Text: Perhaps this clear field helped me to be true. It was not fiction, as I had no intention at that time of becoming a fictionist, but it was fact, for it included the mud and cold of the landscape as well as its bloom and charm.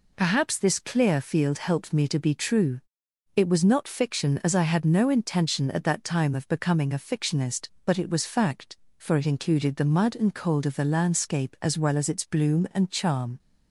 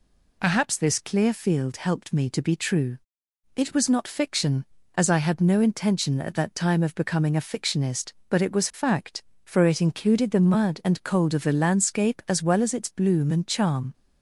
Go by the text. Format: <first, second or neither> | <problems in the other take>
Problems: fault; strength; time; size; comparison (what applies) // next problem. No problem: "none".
neither | none